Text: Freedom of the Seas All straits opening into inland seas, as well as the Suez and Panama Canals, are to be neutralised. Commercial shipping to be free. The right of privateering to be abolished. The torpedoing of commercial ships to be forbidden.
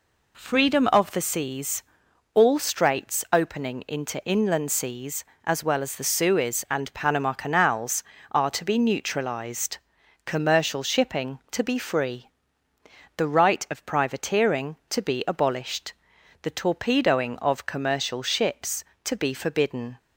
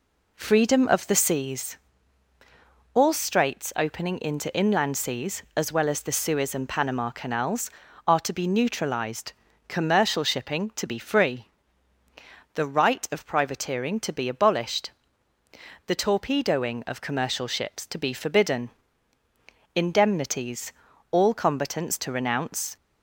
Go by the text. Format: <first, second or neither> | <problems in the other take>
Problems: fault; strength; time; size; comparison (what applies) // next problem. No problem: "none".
first | pauses between "Seas" and "All"; at 1.7 s; 1.1 s long; noticeable in the first // goes on to say "Indemnities All combatants to renounce"; strong; from 19.7 s on; 3.0 s long